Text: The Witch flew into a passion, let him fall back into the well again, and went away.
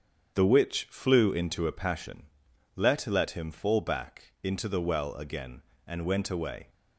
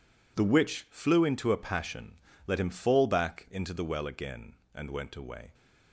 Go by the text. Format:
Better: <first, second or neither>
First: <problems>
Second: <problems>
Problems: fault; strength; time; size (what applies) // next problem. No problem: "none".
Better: second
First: starts louder than the rest; strong; until 1.3 s; 8 dB // says "let" twice; at 3.0 s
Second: none